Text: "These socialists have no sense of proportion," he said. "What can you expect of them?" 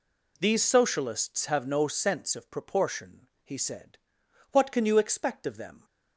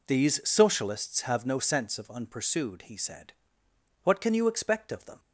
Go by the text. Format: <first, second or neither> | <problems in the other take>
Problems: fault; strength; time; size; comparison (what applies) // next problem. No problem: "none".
first | says "unpursued" for "proportion"; at 2.0 s